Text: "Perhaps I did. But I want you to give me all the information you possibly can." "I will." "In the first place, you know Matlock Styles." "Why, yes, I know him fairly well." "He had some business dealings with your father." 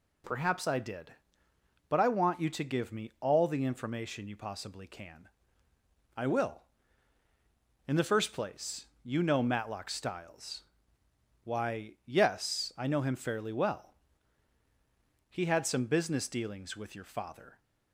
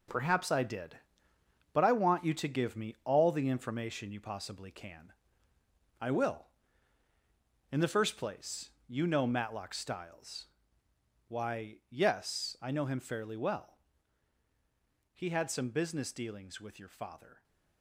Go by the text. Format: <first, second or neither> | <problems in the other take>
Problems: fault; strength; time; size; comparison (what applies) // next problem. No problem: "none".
first | gets quieter; strong; throughout; 8.5 dB